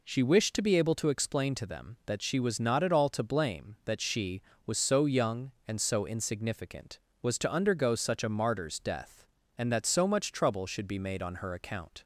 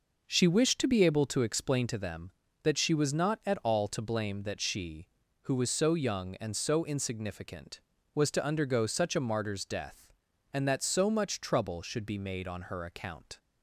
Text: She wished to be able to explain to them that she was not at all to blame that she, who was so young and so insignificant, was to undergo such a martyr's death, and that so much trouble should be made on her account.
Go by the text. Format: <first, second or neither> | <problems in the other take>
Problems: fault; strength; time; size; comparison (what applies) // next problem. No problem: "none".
second | skips "who"; at 4.5 s